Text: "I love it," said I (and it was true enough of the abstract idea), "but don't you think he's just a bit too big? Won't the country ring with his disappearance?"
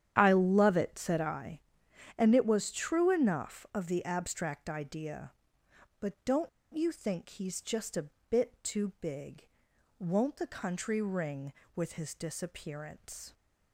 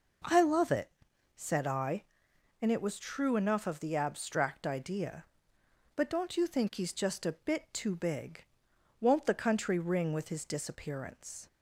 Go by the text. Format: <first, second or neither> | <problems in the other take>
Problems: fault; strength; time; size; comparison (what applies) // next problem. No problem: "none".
second | starts louder than the rest; strong; until 1.1 s; 10 dB // pauses between "don't" and "you"; slight; at 6.4 s; 0.28 s long // pauses between "a" and "bit"; slight; at 8.0 s; 0.22 s long